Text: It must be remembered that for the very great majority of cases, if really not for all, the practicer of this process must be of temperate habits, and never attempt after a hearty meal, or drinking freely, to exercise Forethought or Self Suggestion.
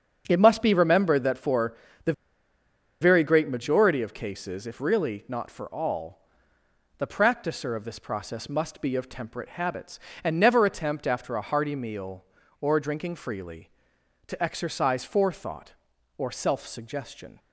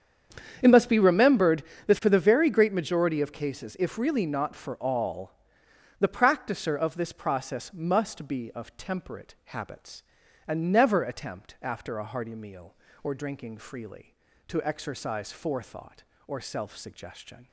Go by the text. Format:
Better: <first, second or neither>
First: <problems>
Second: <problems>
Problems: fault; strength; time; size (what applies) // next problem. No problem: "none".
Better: second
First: starts louder than the rest; strong; until 1.2 s; 7 dB // pauses between "for" and "the"; slight; at 1.7 s; 0.28 s long // pauses between "the" and "very"; noticeable; at 2.1 s; 0.89 s long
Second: starts louder than the rest; strong; until 1.6 s; 8 dB